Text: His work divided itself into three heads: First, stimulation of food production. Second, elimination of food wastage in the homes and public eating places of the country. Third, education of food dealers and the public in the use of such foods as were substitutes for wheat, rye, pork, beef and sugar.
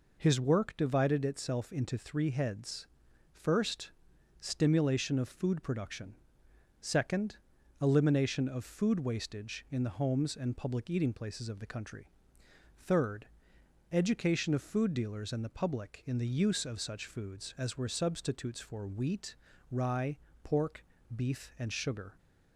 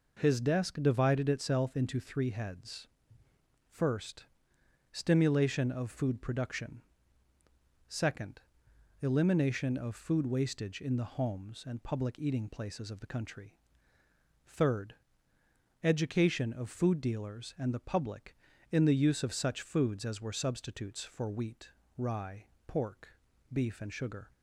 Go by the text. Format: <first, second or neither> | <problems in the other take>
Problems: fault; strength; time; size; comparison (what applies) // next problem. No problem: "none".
first | says "desk" for "work"; at 0.3 s